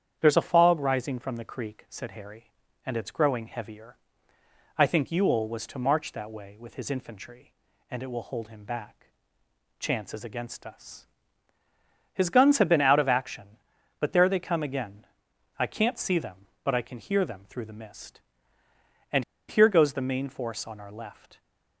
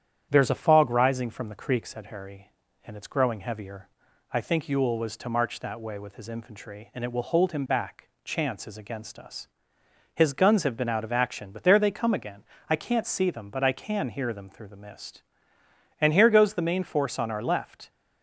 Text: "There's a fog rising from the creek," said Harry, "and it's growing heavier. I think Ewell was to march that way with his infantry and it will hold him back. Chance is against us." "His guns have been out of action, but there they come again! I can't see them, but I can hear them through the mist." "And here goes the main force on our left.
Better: second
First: starts louder than the rest; strong; until 1.2 s; 8.5 dB // pauses between "And" and "here"; slight; at 19.2 s; 0.24 s long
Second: starts louder than the rest; strong; until 1.3 s; 9.5 dB

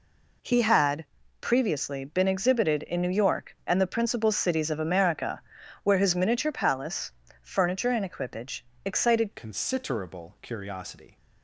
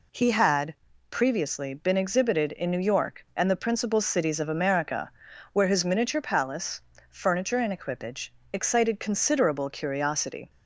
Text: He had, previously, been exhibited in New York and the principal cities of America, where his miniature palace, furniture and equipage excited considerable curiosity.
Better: second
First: pauses between "equipage" and "excited"; slight; at 8.6 s; 0.22 s long // changes voice at "considerable"; from 9.3 s on; 1.8 s long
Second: pauses between "equipage" and "excited"; slight; at 8.3 s; 0.22 s long

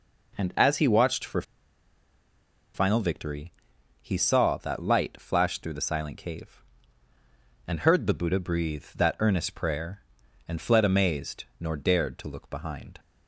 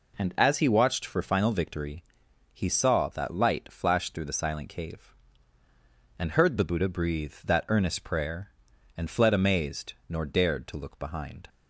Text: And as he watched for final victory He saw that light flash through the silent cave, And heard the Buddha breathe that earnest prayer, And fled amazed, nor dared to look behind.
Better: second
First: pauses between "for" and "final"; strong; at 1.4 s; 1.3 s long // pauses between "victory" and "He"; noticeable; at 3.5 s; 0.50 s long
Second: pauses between "victory" and "He"; noticeable; at 2.0 s; 0.50 s long

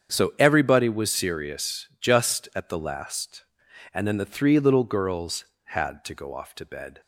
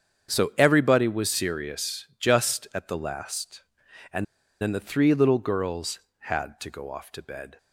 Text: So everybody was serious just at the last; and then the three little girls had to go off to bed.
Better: first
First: starts louder than the rest; strong; until 1.1 s; 7.5 dB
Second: starts louder than the rest; strong; until 1.3 s; 7.5 dB // pauses between "and" and "then"; at 4.2 s; 0.38 s long

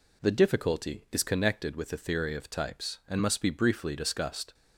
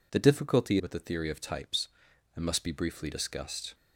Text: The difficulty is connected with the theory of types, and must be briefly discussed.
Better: first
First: none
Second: skips "is connected"; at 0.7 s

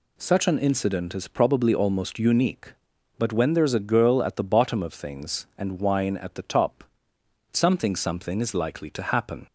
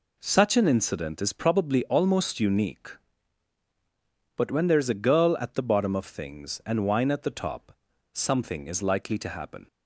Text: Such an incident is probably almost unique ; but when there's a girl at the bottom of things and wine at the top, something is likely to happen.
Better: second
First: says "something" twice; at 7.9 s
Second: none

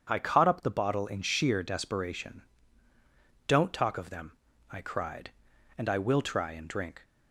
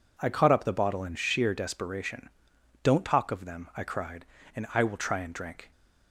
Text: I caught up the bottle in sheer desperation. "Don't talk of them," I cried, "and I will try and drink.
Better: neither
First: none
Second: none

